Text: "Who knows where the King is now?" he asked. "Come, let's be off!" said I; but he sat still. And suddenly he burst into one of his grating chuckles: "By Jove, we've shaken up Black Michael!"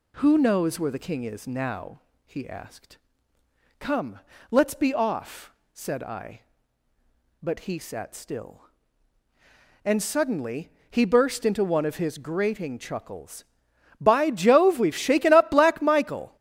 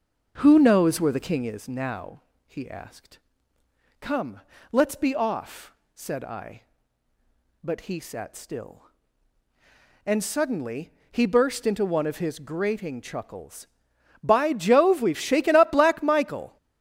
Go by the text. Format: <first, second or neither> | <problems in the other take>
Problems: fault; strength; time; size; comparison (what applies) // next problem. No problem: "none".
first | starts louder than the rest; noticeable; until 1.6 s; 6 dB // pauses between "suddenly" and "he"; slight; at 10.9 s; 0.18 s long; slight in the first